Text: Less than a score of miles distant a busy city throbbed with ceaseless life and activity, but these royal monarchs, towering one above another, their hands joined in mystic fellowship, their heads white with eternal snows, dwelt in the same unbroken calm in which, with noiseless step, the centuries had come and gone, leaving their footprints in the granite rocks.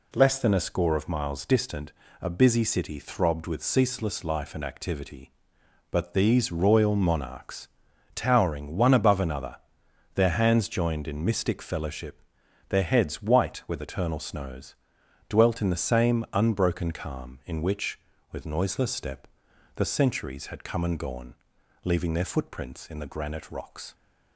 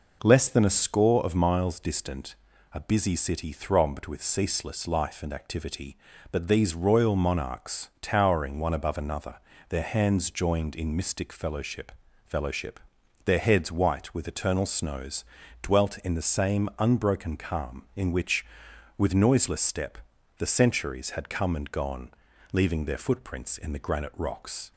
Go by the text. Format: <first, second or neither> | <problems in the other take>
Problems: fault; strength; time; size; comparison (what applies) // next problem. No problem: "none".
first | pauses between "distant" and "a"; at 2.3 s; 0.38 s long; slight in the first // says "fellowship" twice; at 12.2 s